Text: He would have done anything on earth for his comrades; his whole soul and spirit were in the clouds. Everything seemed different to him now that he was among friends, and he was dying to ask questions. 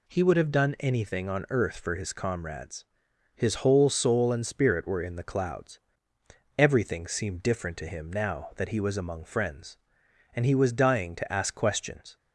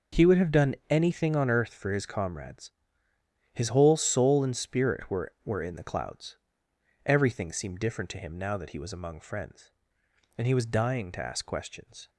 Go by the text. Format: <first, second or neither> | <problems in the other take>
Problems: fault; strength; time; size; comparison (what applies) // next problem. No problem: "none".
first | pauses between "done" and "anything"; slight; at 0.7 s; 0.16 s long // says "were" twice; at 5.4 s